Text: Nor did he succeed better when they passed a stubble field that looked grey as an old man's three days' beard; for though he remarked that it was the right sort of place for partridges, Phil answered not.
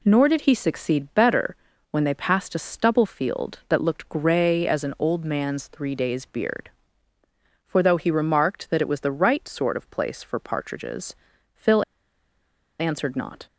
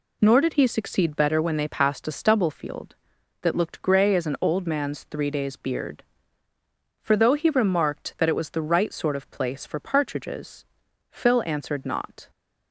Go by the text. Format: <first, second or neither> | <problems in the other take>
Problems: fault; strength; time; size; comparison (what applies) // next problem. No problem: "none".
second | pauses between "better" and "when"; slight; at 1.5 s; 0.36 s long // pauses between "Phil" and "answered"; noticeable; at 11.8 s; 0.96 s long